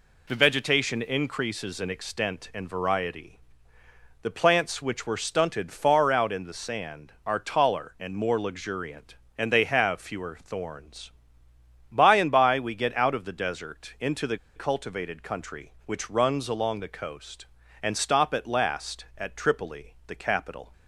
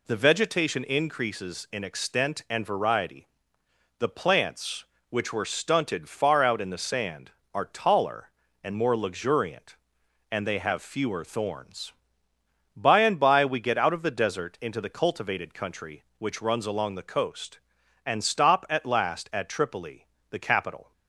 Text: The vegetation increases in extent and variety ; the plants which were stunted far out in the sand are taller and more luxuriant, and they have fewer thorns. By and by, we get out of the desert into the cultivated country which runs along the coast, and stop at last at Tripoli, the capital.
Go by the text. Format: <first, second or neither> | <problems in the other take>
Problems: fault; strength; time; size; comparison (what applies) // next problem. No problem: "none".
second | pauses between "the" and "cultivated"; slight; at 14.3 s; 0.18 s long